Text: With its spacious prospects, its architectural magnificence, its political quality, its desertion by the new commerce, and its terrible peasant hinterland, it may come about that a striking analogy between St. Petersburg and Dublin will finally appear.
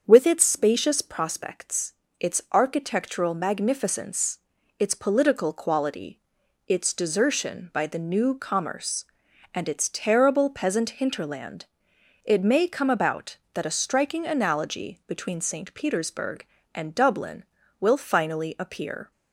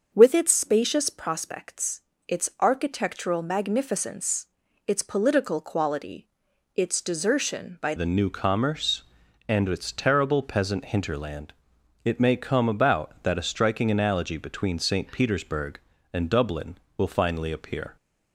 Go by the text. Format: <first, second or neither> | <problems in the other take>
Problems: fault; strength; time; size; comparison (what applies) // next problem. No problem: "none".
first | starts louder than the rest; until 1.1 s; 6.5 dB; strong in the first // changes voice at "the"; from 7.9 s on; 10.0 s long